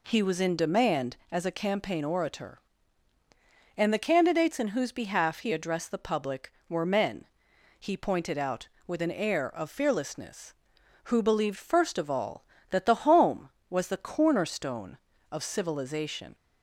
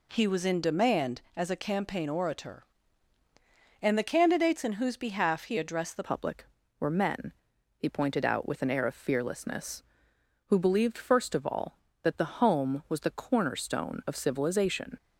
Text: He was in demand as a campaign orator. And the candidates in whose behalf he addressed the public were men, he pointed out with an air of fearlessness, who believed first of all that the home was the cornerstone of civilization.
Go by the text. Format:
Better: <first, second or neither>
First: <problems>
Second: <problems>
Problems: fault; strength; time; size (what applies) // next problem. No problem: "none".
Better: first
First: none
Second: changes voice at "public"; from 6.0 s on; 8.9 s long